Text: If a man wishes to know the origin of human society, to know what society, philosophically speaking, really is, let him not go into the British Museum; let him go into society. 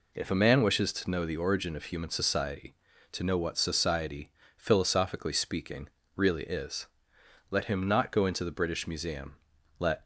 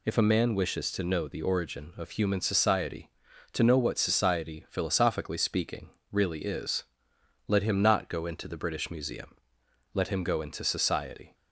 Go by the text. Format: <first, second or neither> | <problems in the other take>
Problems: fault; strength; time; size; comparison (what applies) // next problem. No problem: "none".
second | stops before "him go into society"; at 10.0 s